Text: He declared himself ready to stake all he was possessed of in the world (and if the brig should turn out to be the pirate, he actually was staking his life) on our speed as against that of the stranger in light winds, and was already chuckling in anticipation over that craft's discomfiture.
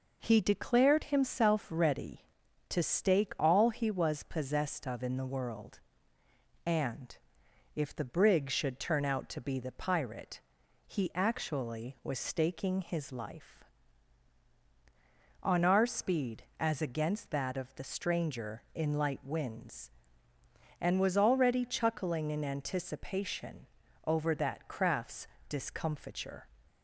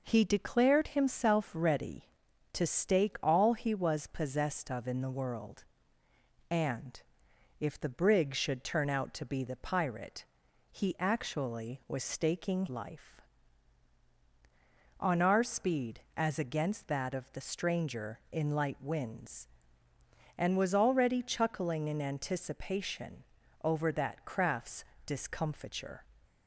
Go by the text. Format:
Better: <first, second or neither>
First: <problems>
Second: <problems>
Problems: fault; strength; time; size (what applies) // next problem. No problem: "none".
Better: first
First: pauses between "and" and "if"; noticeable; at 7.1 s; 0.58 s long // pauses between "anticipation" and "over"; at 23.6 s; 0.38 s long // pauses between "craft's" and "discomfiture"; slight; at 25.2 s; 0.20 s long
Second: pauses between "and" and "if"; noticeable; at 6.9 s; 0.58 s long // skips "his"; at 12.6 s // pauses between "anticipation" and "over"; at 23.2 s; 0.38 s long // pauses between "craft's" and "discomfiture"; slight; at 24.8 s; 0.20 s long